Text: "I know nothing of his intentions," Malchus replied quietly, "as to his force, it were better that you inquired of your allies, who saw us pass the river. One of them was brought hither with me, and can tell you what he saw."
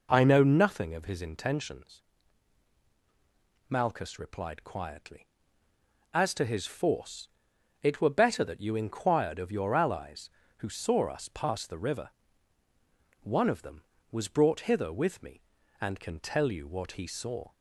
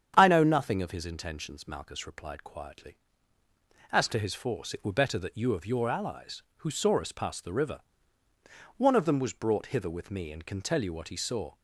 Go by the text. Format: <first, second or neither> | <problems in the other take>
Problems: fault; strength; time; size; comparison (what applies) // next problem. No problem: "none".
first | starts louder than the rest; strong; until 1.1 s; 8.5 dB // skips "inquired"; at 5.5 s